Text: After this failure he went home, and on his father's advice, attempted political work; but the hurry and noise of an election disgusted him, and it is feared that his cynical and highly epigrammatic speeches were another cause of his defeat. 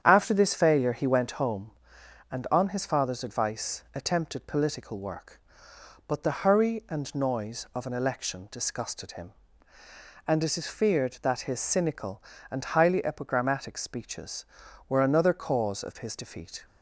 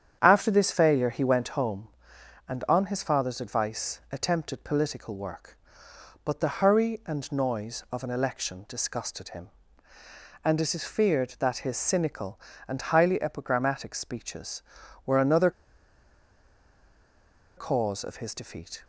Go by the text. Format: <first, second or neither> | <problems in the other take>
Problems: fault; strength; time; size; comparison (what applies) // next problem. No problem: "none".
first | starts louder than the rest; strong; until 1.2 s; 8.5 dB; strong in the first // pauses between "another" and "cause"; strong; at 15.5 s; 2.0 s long